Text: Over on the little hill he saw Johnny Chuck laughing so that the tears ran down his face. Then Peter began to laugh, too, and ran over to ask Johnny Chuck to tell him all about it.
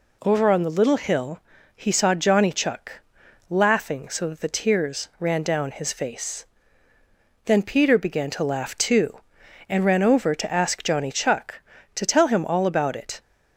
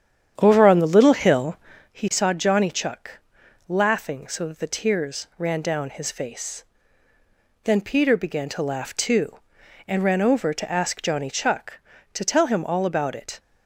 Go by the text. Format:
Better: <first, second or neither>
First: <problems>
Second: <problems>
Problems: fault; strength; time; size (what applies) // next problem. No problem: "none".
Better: first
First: pauses between "hill" and "he"; at 1.3 s; 0.38 s long // pauses between "Chuck" and "laughing"; noticeable; at 2.9 s; 0.50 s long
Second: starts louder than the rest; strong; until 1.9 s; 9 dB // pauses between "hill" and "he"; at 1.5 s; 0.38 s long // pauses between "Chuck" and "laughing"; noticeable; at 3.1 s; 0.50 s long